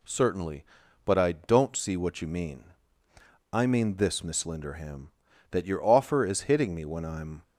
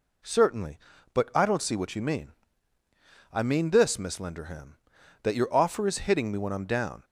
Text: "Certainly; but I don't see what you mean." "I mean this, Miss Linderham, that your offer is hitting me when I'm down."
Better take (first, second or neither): second